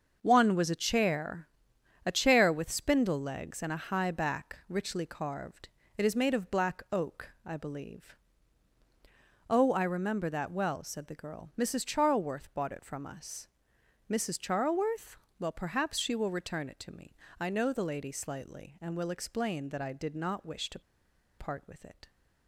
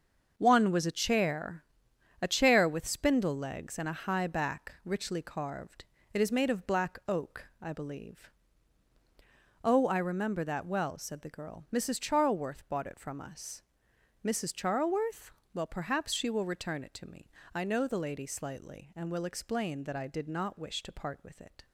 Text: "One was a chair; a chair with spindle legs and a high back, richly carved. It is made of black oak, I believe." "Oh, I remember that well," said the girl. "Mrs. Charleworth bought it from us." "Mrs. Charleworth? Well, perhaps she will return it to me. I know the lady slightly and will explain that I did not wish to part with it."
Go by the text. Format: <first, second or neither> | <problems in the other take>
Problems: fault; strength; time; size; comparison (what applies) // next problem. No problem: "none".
second | starts louder than the rest; until 1.2 s; 6.5 dB; also in the second // pauses between "to" and "part"; noticeable; at 20.7 s; 0.59 s long